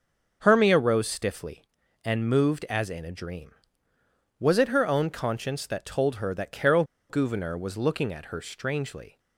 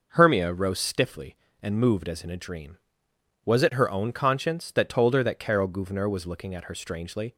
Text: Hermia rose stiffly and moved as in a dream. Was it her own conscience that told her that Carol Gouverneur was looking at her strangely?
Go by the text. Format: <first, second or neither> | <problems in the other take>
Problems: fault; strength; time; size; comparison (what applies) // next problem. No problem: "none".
second | starts louder than the rest; until 1.4 s; 6.5 dB // pauses between "Carol" and "Gouverneur"; slight; at 6.8 s; 0.26 s long